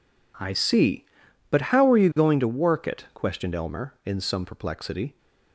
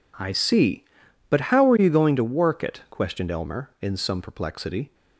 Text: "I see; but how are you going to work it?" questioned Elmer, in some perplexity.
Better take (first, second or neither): neither